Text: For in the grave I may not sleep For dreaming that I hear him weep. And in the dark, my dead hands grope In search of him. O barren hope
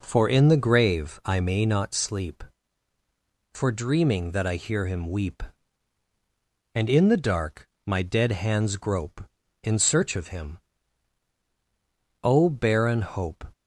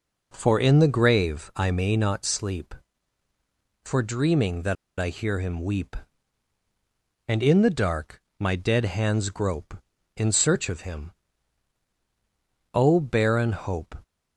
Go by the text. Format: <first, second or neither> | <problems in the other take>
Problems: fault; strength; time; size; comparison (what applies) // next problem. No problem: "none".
first | pauses between "that" and "I"; slight; at 4.7 s; 0.25 s long